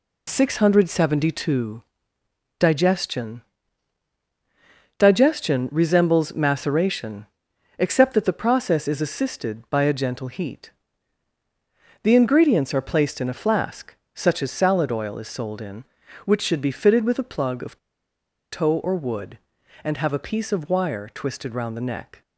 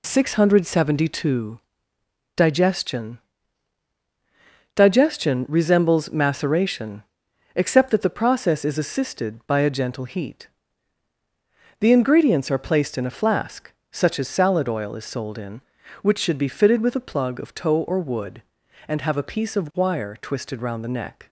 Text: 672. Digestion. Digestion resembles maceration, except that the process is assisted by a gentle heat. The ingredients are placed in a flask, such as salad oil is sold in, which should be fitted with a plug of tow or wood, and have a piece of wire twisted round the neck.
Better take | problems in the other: second | pauses between "of" and "tow"; noticeable; at 17.7 s; 0.73 s long

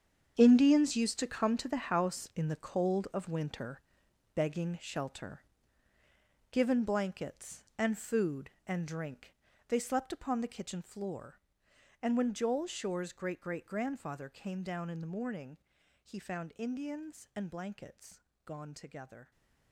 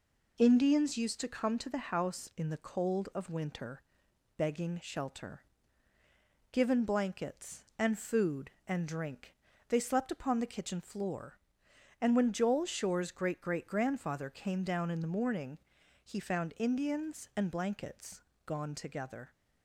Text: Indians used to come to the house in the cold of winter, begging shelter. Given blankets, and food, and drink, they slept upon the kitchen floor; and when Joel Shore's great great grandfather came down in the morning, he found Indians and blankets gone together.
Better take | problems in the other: second | gets quieter; strong; throughout; 13 dB // pauses between "blankets" and "gone"; slight; at 18.2 s; 0.24 s long; slight in the second

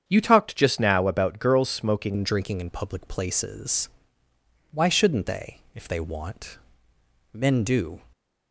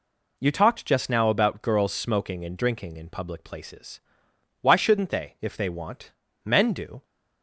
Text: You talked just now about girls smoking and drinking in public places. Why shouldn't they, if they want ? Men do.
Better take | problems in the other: second | starts louder than the rest; strong; until 1.0 s; 8 dB // changes voice at "and"; from 2.1 s on; 5.9 s long // stays silent after the last word; slight; from 7.9 s on; 0.6 s long

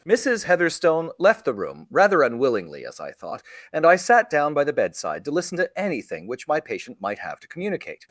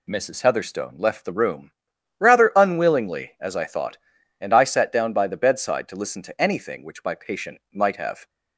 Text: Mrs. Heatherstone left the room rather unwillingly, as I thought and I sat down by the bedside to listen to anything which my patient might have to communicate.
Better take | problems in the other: first | pauses between "room" and "rather"; noticeable; at 1.7 s; 0.48 s long // pauses between "patient" and "might"; slight; at 7.5 s; 0.16 s long // stops before "to communicate"; at 8.2 s

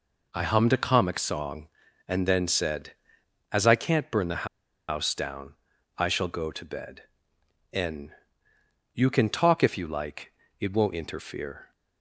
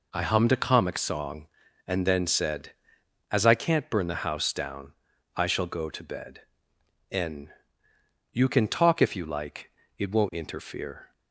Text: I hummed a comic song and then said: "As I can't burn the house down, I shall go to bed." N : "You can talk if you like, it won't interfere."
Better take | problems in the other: second | pauses between "the" and "house"; at 4.4 s; 0.42 s long

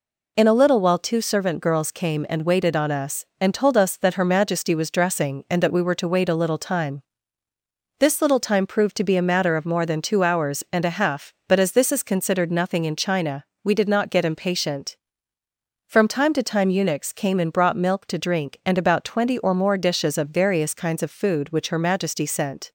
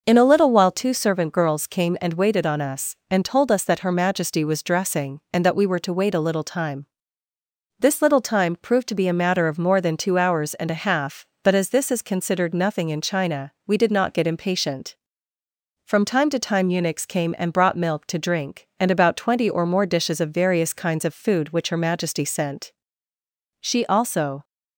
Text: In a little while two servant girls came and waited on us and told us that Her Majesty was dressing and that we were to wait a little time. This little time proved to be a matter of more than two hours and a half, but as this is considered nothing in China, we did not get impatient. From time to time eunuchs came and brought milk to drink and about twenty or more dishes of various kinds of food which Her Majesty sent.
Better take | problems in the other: first | goes on to say "She also"; noticeable; from 23.6 s on; 0.82 s long

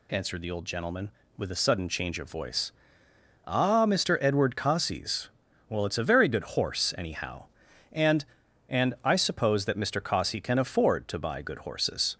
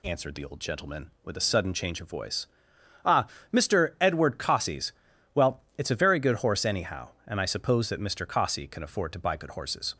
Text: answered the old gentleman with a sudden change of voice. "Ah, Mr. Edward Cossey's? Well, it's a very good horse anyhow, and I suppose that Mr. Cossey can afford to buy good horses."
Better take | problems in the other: second | says "and" twice; at 8.6 s

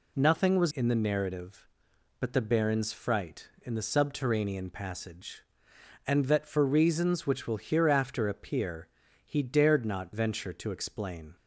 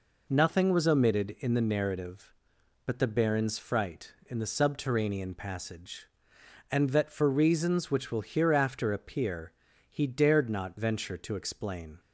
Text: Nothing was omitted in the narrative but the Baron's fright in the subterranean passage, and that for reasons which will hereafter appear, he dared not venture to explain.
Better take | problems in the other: second | skips "omitted"; at 0.7 s

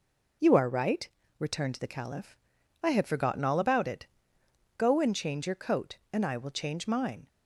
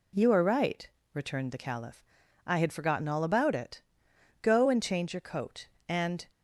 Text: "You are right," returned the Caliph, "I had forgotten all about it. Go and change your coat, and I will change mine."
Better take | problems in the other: first | stops before "I will change mine"; at 6.3 s

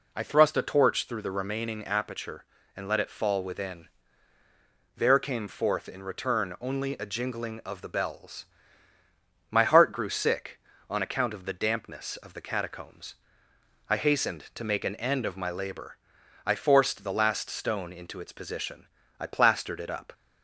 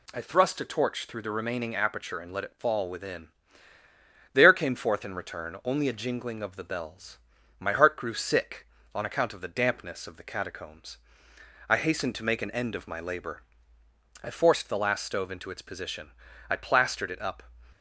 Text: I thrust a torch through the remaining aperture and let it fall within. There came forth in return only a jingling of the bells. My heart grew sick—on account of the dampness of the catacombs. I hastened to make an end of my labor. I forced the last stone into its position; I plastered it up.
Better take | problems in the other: first | says "stove" for "stone"; at 15.0 s

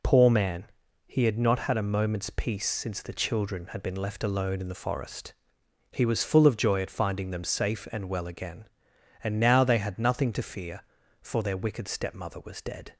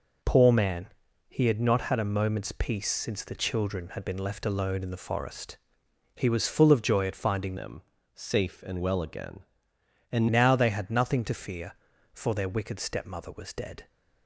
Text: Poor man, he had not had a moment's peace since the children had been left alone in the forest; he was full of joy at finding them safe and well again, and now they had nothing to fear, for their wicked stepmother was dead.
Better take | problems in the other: first | changes voice from "them" to "and"; from 7.5 to 10.2 s; 2.7 s long // pauses between "them" and "safe"; slight; at 7.8 s; 0.32 s long

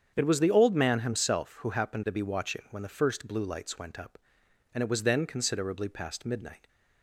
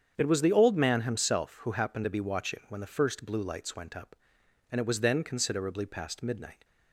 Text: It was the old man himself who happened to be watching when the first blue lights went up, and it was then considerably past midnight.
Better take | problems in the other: neither | starts louder than the rest; strong; the same in both

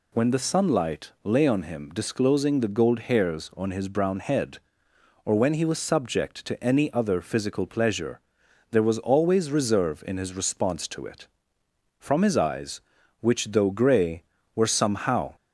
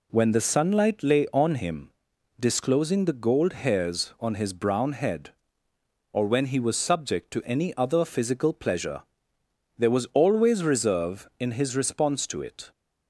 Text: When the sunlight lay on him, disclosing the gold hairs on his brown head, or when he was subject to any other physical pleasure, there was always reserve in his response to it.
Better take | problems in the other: second | goes on to say "From his eyes which though gray were somehow"; strong; from 11.9 s on; 3.3 s long

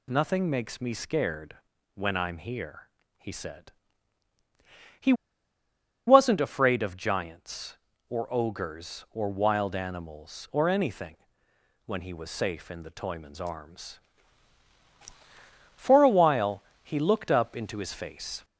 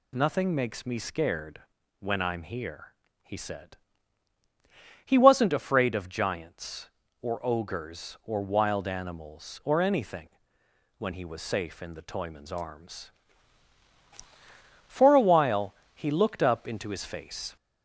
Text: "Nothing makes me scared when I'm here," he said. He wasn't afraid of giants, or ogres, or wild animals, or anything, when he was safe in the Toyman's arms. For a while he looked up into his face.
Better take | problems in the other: second | pauses between "scared" and "when"; slight; at 1.5 s; 0.36 s long; slight in the second // pauses between "He" and "wasn't"; noticeable; at 5.1 s; 0.94 s long // pauses between "while" and "he"; slight; at 16.6 s; 0.20 s long; slight in the second

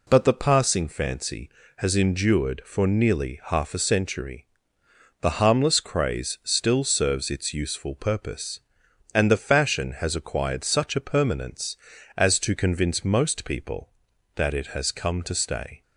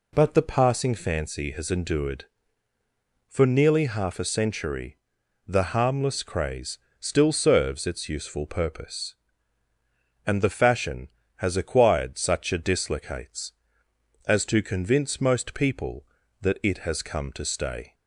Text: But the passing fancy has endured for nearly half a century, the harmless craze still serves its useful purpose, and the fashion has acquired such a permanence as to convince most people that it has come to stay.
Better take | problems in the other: first | pauses between "craze" and "still"; slight; at 6.7 s; 0.22 s long // says "dislocates" for "permanence"; at 12.5 s

